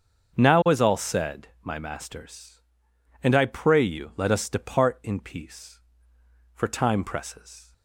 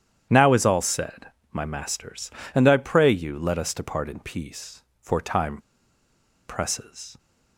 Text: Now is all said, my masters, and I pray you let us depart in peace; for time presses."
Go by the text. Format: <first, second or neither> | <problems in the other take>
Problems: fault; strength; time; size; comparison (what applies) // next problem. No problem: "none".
first | starts louder than the rest; strong; until 1.5 s; 9.5 dB; also in the first // pauses between "time" and "presses"; noticeable; at 5.5 s; 0.90 s long